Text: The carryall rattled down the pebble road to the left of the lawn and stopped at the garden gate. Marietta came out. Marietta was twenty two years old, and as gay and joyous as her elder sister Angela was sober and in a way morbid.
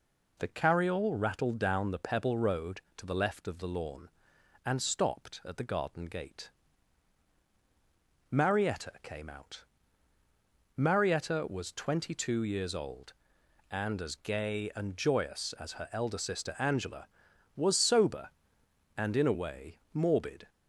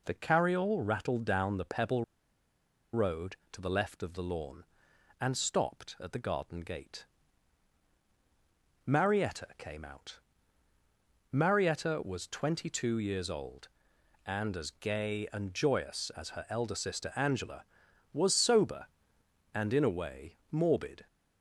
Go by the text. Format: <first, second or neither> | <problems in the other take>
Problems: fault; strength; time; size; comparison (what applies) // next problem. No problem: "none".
first | pauses between "pebble" and "road"; noticeable; at 2.0 s; 0.89 s long